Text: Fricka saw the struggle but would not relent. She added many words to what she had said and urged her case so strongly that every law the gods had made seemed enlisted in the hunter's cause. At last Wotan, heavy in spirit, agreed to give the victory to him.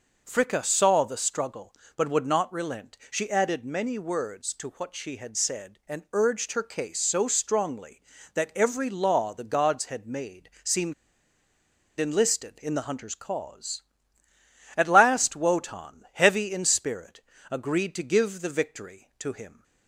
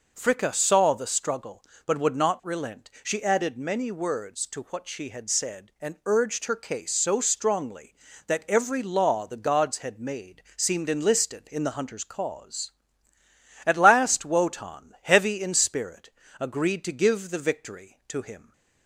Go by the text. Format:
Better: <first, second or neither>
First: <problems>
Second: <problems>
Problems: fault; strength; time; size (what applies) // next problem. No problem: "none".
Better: second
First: pauses between "seemed" and "enlisted"; at 10.9 s; 1.0 s long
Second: none